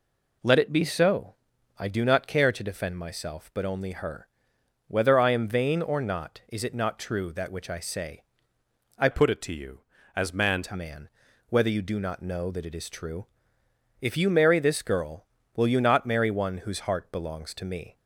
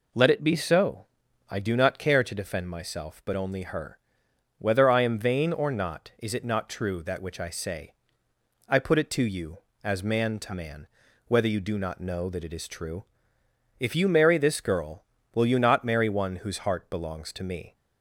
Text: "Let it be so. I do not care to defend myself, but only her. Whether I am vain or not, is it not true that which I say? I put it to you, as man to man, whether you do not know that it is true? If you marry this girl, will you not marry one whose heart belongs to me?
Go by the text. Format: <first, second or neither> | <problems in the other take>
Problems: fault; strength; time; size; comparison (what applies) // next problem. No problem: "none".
second | changes voice from "put" to "man"; from 9.1 to 10.6 s; 1.5 s long